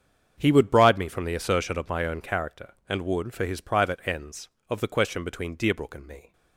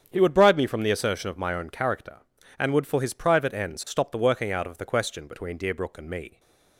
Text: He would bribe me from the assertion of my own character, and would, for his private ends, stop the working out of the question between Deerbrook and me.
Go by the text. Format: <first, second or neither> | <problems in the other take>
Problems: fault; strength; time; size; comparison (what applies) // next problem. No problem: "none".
second | starts louder than the rest; strong; until 1.3 s; 7.5 dB; strong in the second // skips "stop the working out"; at 4.5 s